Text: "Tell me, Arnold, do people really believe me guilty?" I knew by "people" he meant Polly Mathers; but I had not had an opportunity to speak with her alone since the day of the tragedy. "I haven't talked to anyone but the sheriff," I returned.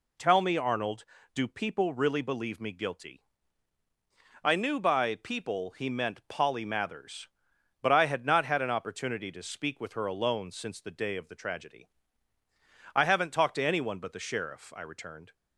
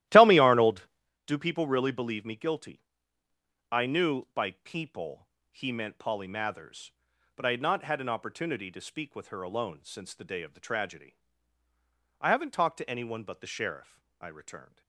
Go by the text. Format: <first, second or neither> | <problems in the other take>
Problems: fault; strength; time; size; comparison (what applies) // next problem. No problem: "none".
first | starts louder than the rest; strong; until 1.1 s; 14.5 dB // pauses between "people" and "he"; slight; at 5.2 s; 0.24 s long